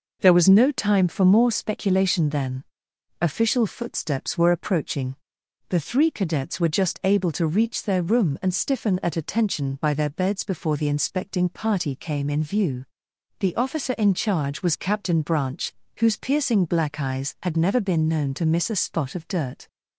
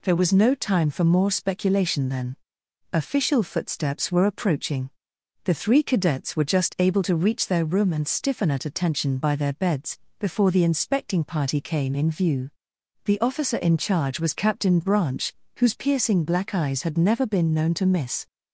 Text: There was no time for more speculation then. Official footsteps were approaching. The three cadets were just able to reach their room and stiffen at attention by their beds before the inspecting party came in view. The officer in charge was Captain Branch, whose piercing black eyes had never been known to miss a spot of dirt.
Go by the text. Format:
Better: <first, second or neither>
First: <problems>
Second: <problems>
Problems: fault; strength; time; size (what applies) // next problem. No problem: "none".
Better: first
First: none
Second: pauses between "beds" and "before"; slight; at 9.9 s; 0.20 s long // stops before "a spot of dirt"; at 18.2 s